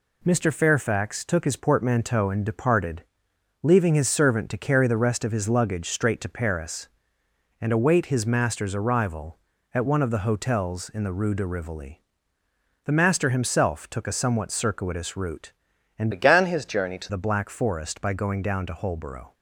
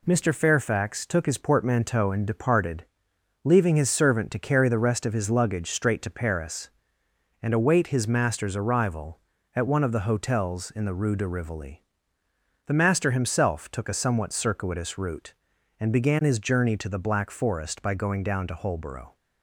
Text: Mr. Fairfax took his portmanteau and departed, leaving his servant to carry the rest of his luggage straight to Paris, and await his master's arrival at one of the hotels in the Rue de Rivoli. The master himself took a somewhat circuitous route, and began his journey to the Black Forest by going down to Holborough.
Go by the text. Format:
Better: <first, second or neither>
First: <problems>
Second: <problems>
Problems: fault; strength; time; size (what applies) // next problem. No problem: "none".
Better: second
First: changes voice from "began" to "to"; from 16.1 to 17.0 s; 0.9 s long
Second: none